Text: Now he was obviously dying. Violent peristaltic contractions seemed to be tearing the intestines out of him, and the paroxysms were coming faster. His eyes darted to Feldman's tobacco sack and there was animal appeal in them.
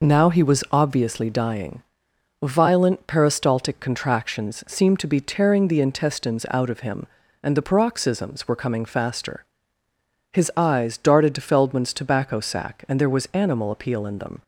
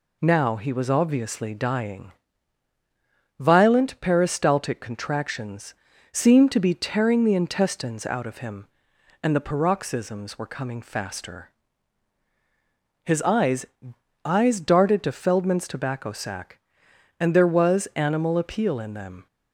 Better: first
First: none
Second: pauses between "contractions" and "seemed"; slight; at 5.7 s; 0.36 s long // says "eyes" twice; at 14.2 s

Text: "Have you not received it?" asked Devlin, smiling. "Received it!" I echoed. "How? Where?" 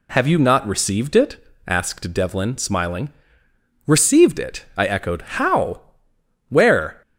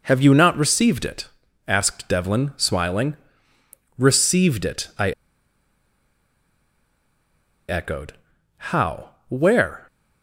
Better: first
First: none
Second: pauses between "I" and "echoed"; strong; at 5.1 s; 2.5 s long

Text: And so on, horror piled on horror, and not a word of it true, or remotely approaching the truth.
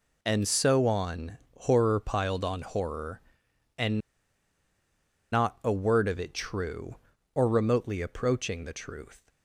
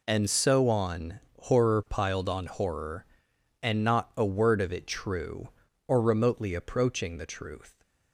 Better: second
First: pauses between "and" and "not"; strong; at 3.9 s; 1.3 s long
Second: none

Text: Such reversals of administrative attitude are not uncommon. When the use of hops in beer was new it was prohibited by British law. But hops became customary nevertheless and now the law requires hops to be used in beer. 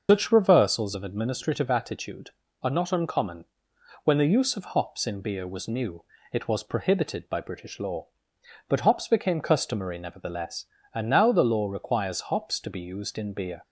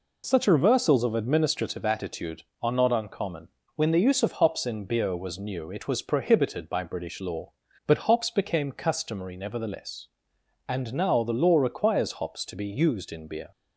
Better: second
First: loses the start of "Such"; at 0.0 s; 150 ms // starts louder than the rest; noticeable; until 1.1 s; 6 dB // pauses between "new" and "it"; slight; at 6.0 s; 0.26 s long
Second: none

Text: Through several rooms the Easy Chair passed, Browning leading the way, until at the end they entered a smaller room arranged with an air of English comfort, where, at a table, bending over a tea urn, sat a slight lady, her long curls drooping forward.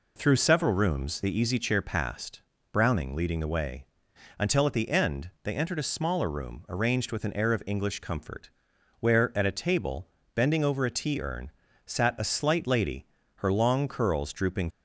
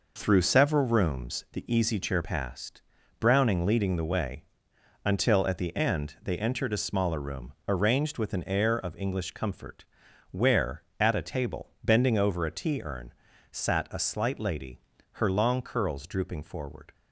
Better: second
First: stops before "forward"; at 14.6 s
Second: none

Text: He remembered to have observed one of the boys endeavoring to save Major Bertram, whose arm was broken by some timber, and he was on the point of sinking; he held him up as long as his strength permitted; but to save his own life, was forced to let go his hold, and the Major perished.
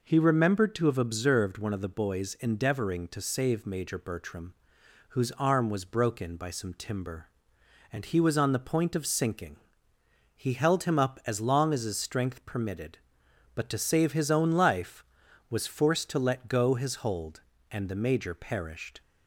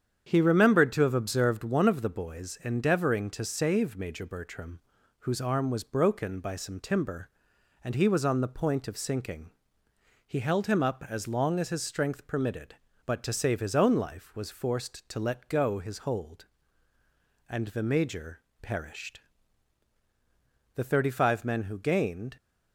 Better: first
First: none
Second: starts louder than the rest; strong; until 1.2 s; 8 dB // pauses between "Major" and "perished"; slight; at 18.4 s; 0.20 s long // goes on to say "The thirty five men who gained"; from 20.7 s on; 1.6 s long

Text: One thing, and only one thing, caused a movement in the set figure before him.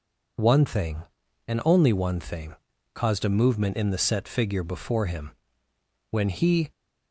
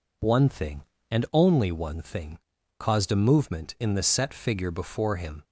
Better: second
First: goes on to say "When he"; from 6.1 s on; 0.60 s long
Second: none

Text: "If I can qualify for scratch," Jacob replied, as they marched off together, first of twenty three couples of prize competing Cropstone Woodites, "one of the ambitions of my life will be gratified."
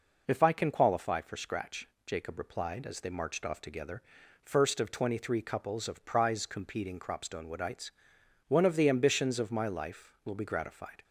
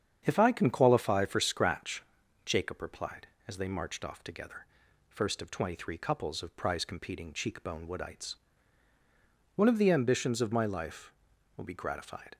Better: first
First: none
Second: starts louder than the rest; strong; until 1.2 s; 8 dB // says "Cheekbone" for "Cropstone"; at 7.3 s

